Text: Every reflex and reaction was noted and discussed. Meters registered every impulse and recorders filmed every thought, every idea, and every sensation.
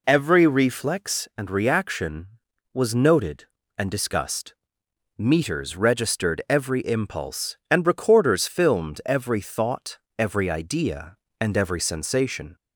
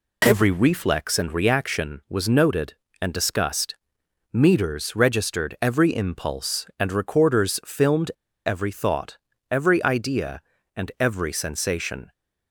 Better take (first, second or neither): first